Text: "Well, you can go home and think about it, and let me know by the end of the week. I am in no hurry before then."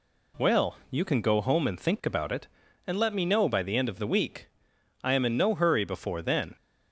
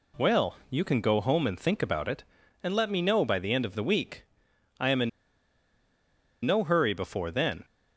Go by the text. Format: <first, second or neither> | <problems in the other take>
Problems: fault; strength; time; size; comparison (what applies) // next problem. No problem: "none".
first | pauses between "in" and "no"; strong; at 5.0 s; 1.3 s long